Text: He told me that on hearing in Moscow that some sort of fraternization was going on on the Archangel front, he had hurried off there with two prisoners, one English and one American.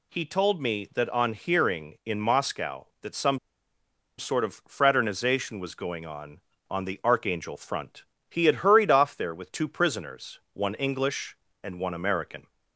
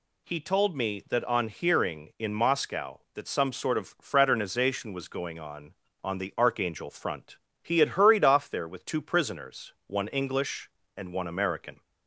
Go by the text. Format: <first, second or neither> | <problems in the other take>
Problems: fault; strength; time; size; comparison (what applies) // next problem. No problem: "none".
second | pauses between "some" and "sort"; noticeable; at 3.3 s; 0.79 s long